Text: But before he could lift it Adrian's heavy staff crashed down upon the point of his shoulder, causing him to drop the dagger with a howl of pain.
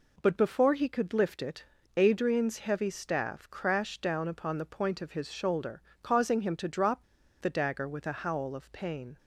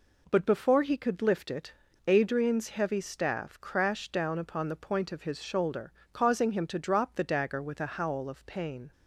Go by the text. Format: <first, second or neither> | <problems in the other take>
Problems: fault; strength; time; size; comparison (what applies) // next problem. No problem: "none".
second | pauses between "it" and "Adrian's"; slight; at 1.6 s; 0.32 s long; slight in the second // pauses between "drop" and "the"; at 7.0 s; 0.37 s long